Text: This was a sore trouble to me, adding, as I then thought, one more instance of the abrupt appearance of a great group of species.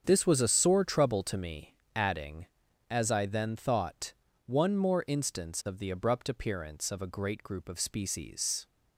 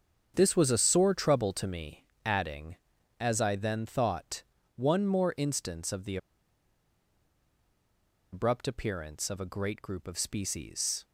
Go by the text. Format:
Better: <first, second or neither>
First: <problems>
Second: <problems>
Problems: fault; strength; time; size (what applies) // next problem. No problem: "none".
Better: first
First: starts louder than the rest; strong; until 1.0 s; 7.5 dB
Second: starts louder than the rest; strong; until 1.3 s; 7.5 dB // pauses between "the" and "abrupt"; strong; at 6.1 s; 2.1 s long